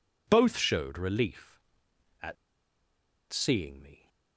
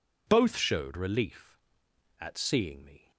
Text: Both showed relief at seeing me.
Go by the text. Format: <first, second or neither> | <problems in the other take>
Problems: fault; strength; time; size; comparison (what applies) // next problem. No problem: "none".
second | pauses between "at" and "seeing"; noticeable; at 2.3 s; 0.96 s long